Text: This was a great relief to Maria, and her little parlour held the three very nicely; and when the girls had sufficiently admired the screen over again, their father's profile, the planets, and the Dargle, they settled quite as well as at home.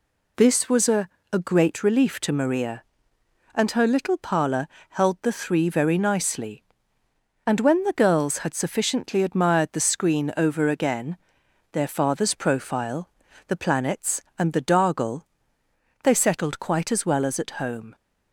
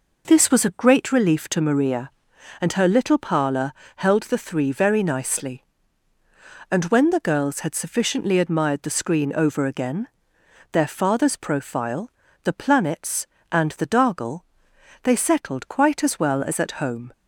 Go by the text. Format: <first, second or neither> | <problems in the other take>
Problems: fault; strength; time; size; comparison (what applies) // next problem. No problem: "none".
second | says "a" twice; at 1.3 s // pauses between "parlour" and "held"; slight; at 4.6 s; 0.22 s long; slight in the second